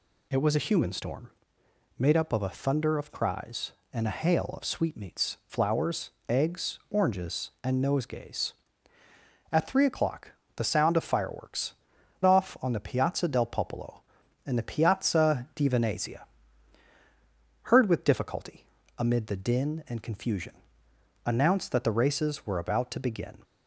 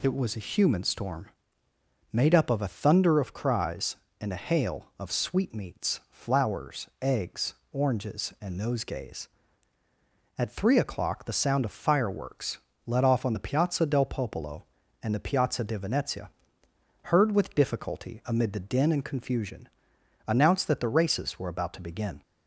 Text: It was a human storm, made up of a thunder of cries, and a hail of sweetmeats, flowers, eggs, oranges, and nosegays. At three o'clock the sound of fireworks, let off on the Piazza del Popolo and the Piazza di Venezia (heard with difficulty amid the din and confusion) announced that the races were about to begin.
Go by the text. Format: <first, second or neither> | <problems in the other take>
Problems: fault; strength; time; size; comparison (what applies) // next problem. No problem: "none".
second | pauses between "o'clock" and "the"; slight; at 10.3 s; 0.24 s long // skips "let"; at 11.9 s // pauses between "difficulty" and "amid"; slight; at 18.6 s; 0.34 s long